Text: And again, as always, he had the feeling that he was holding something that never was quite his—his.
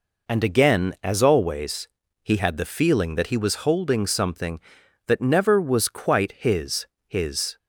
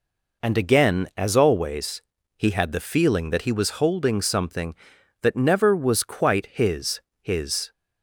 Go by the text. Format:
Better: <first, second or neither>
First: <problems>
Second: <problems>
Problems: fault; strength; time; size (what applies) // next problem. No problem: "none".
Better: neither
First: none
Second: none